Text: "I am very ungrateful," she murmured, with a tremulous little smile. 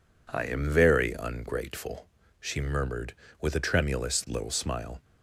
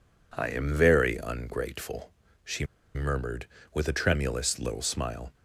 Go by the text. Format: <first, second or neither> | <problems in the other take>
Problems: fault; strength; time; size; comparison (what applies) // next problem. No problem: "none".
first | pauses between "she" and "murmured"; slight; at 2.6 s; 0.30 s long